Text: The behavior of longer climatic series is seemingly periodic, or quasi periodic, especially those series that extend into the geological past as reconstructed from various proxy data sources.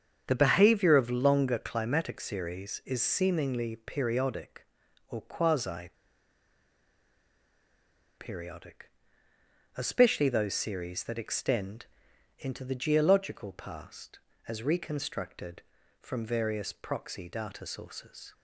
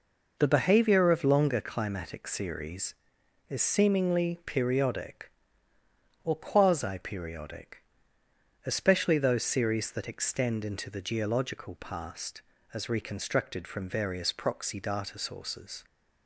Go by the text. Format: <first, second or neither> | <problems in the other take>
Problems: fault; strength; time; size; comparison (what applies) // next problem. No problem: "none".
second | starts louder than the rest; strong; until 1.2 s; 7.5 dB // pauses between "quasi" and "periodic"; strong; at 5.9 s; 2.2 s long // pauses between "extend" and "into"; noticeable; at 11.8 s; 0.52 s long